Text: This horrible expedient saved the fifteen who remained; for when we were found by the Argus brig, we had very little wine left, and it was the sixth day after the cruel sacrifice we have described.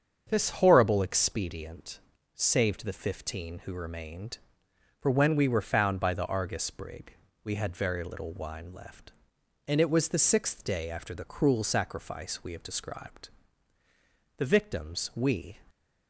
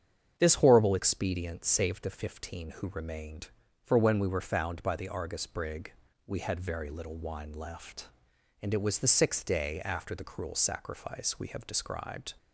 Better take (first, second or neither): second